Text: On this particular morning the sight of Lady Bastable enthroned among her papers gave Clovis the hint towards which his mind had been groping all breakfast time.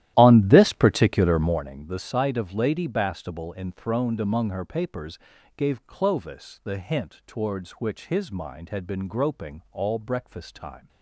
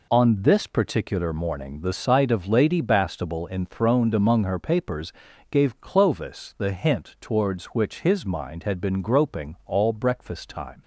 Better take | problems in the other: second | starts louder than the rest; strong; until 1.7 s; 13.5 dB // pauses between "papers" and "gave"; at 5.1 s; 0.38 s long; also in the second

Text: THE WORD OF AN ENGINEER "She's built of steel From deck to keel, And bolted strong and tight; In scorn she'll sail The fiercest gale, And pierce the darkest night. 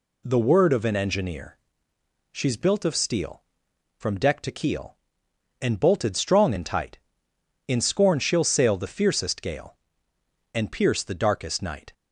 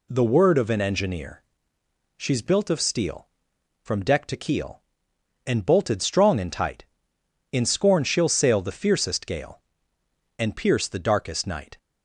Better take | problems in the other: neither | pauses between "ENGINEER" and "She's"; noticeable; the same in both

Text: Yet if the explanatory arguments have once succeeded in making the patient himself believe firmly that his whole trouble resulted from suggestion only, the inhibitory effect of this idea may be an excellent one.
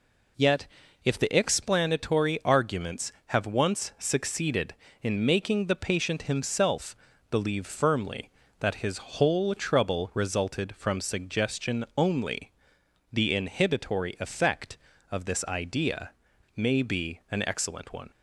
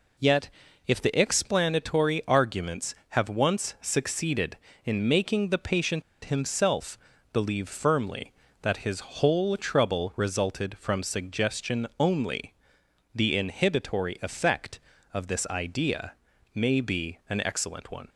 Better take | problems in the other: first | pauses between "Yet" and "if"; at 0.4 s; 0.38 s long; also in the first // pauses between "patient" and "himself"; slight; at 6.0 s; 0.22 s long // pauses between "himself" and "believe"; slight; at 6.9 s; 0.36 s long; slight in the first // pauses between "idea" and "may"; at 16.1 s; 0.42 s long; noticeable in the first

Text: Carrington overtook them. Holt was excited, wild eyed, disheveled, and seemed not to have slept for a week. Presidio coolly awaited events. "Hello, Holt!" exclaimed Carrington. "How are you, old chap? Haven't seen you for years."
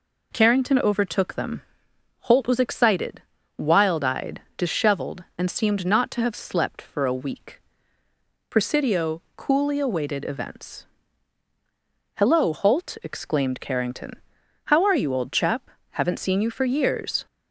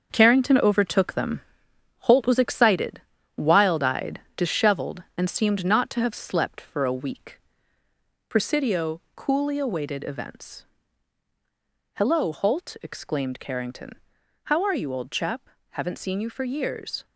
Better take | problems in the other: first | gets quieter; strong; throughout; 7 dB

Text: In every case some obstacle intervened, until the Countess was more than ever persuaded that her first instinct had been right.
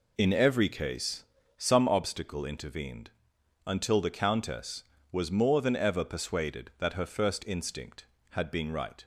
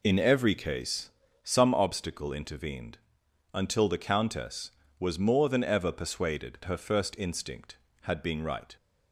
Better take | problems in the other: first | pauses between "case" and "some"; slight; at 1.1 s; 0.34 s long; slight in the first // skips "that"; at 6.6 s

